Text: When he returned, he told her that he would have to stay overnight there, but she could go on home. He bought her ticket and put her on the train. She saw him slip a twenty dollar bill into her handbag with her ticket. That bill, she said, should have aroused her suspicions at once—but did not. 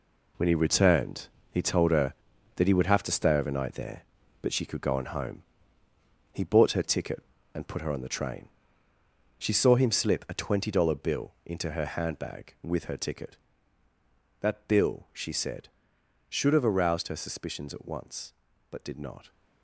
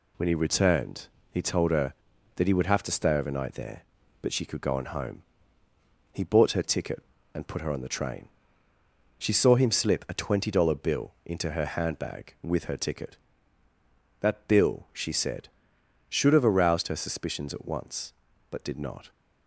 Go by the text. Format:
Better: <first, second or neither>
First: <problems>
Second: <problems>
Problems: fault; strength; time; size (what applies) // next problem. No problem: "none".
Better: second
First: gets quieter; strong; throughout; 9 dB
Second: none